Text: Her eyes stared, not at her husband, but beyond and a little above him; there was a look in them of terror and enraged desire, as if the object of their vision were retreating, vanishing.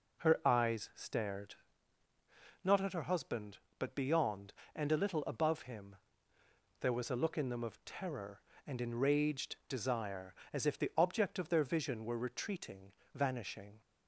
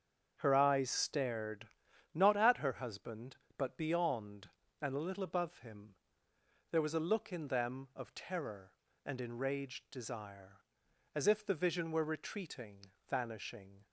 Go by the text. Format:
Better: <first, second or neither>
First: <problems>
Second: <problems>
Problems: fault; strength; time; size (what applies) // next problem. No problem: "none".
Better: first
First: none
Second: starts louder than the rest; strong; until 1.4 s; 7.5 dB // skips "object of their"; at 11.5 s